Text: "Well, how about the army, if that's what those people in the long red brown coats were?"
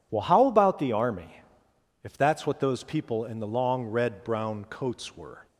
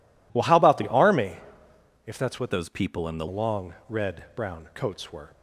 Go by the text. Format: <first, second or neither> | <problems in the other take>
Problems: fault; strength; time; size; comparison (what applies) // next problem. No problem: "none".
first | changes voice from "those" to "the"; from 2.4 to 3.2 s; 0.8 s long